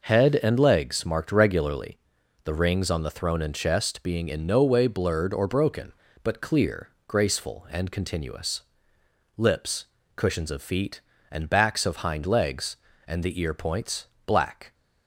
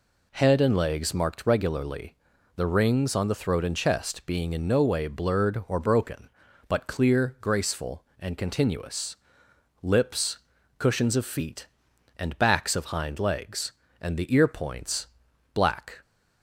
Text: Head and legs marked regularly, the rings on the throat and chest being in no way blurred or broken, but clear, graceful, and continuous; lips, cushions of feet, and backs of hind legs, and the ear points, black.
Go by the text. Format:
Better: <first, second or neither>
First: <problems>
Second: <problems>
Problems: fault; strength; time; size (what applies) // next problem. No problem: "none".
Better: second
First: says "throne" for "throat"; at 3.1 s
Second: none